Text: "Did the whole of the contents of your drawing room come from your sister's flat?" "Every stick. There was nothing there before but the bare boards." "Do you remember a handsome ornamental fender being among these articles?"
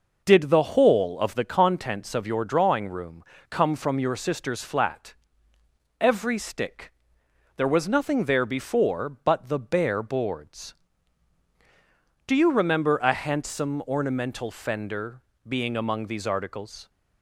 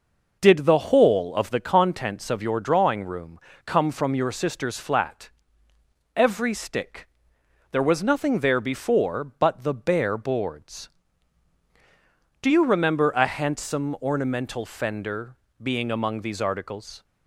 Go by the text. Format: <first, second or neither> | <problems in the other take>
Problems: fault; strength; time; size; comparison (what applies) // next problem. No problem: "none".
neither | pauses between "room" and "come"; slight; the same in both // pauses between "fender" and "being"; slight; the same in both